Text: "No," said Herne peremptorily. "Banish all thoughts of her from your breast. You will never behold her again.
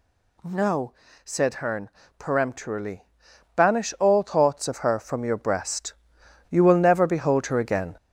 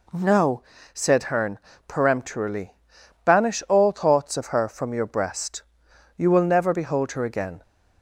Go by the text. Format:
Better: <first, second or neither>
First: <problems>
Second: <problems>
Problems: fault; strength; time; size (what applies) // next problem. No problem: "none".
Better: second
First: gets louder; noticeable; throughout; 4.5 dB // pauses between "Herne" and "peremptorily"; slight; at 1.8 s; 0.28 s long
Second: pauses between "Herne" and "peremptorily"; slight; at 1.5 s; 0.28 s long